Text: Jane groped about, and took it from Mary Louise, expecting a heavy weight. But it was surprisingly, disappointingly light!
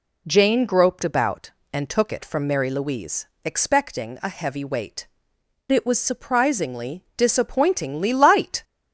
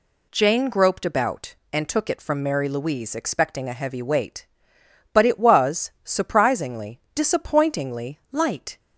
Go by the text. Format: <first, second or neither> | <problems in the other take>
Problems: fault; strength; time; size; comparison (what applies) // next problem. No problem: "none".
second | skips "But"; at 5.3 s